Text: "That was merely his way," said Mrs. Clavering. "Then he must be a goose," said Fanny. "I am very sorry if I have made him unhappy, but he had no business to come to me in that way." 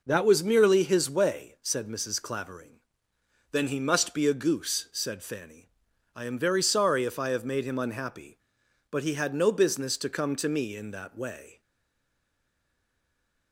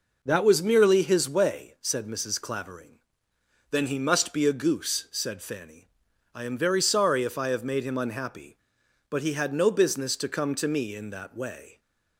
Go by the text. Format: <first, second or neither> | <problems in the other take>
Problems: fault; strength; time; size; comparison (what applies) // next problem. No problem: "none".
second | stays silent after the last word; noticeable; from 11.6 s on; 1.9 s long